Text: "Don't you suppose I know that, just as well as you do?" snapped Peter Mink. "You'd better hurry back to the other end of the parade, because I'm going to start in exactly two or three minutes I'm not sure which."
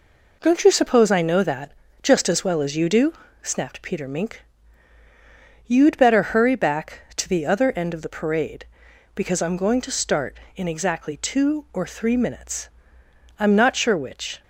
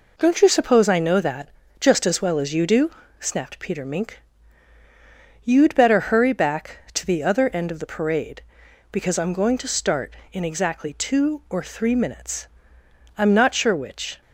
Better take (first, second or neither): neither